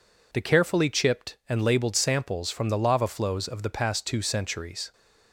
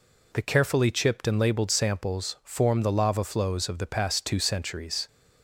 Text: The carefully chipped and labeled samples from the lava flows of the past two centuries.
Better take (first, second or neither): first